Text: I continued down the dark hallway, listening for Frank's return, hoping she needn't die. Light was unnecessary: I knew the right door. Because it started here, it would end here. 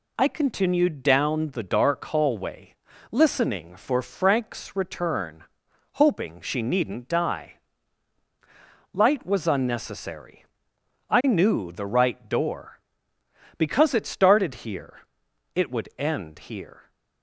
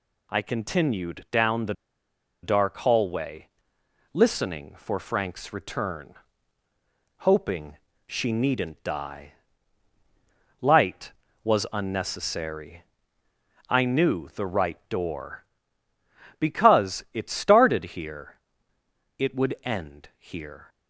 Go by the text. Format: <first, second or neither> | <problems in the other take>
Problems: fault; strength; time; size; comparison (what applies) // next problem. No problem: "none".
first | pauses between "the" and "dark"; noticeable; at 1.7 s; 0.70 s long // pauses between "hoping" and "she"; slight; at 7.7 s; 0.30 s long